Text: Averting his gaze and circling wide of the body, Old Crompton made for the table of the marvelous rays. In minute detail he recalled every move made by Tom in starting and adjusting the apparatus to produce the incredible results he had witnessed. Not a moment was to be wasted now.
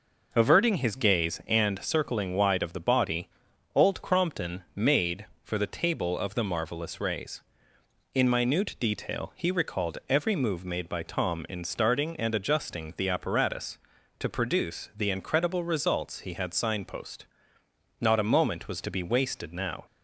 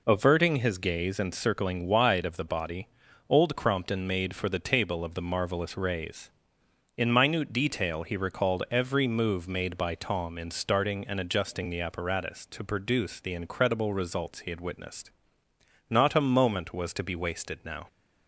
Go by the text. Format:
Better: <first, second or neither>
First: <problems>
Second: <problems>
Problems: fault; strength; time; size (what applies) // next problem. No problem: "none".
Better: second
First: says "signpost" for "witnessed"; at 16.5 s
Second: none